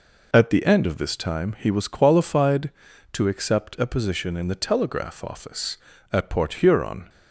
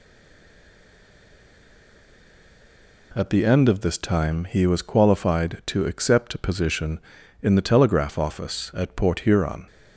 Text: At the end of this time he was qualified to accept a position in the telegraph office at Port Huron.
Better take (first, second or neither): first